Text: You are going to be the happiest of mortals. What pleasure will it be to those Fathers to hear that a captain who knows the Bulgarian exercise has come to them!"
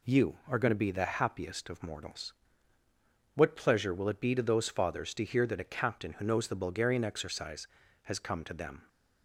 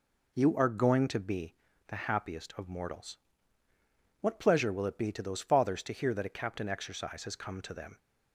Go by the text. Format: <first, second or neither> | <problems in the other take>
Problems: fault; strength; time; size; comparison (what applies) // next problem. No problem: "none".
first | pauses between "be" and "the"; slight; at 1.5 s; 0.32 s long // skips "who knows the Bulgarian"; at 6.6 s